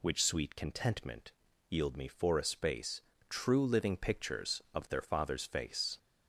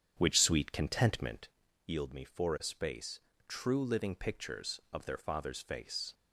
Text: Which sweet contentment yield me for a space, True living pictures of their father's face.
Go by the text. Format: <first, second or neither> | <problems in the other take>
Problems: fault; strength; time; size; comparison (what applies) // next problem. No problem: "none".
first | starts louder than the rest; strong; until 1.6 s; 8.5 dB // pauses between "contentment" and "yield"; at 1.4 s; 0.38 s long; also in the first